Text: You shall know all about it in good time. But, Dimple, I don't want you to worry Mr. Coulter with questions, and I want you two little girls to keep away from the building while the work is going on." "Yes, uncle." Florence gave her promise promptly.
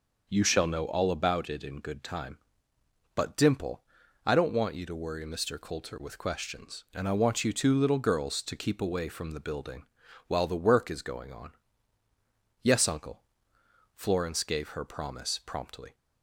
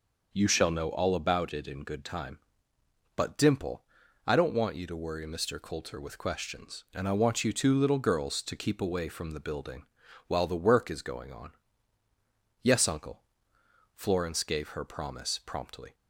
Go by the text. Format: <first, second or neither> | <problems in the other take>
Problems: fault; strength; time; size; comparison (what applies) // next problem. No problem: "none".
neither | pauses between "building" and "while"; the same in both